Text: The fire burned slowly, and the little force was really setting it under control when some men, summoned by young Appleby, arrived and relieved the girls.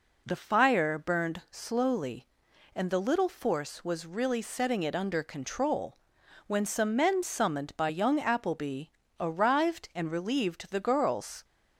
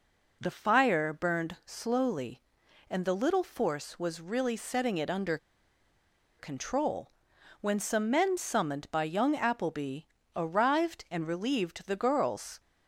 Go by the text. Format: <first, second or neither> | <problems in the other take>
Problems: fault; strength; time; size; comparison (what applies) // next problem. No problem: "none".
first | pauses between "under" and "control"; at 5.3 s; 1.0 s long // pauses between "control" and "when"; noticeable; at 7.0 s; 0.50 s long; noticeable in the first